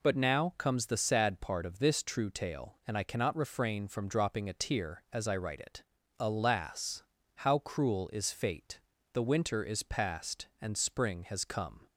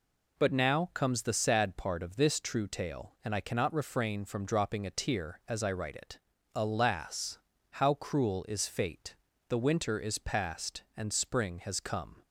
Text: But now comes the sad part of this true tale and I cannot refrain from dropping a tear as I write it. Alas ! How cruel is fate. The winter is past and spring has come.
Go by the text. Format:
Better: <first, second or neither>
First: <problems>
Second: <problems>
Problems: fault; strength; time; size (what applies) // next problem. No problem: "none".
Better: neither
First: none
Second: none